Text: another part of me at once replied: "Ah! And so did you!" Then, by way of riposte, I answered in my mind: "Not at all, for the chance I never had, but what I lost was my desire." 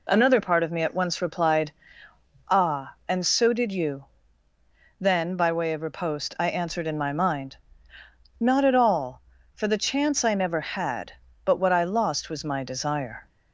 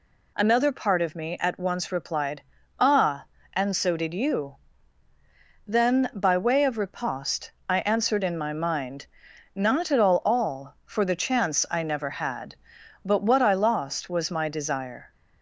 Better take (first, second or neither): first